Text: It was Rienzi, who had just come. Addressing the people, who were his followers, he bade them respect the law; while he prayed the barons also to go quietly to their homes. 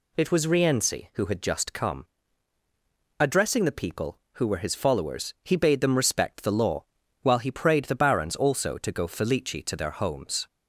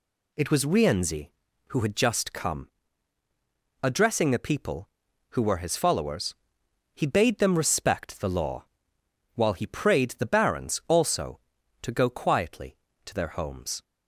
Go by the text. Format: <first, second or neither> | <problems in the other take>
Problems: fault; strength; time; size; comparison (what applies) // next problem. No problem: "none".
second | says "felici" for "quietly"; at 9.0 s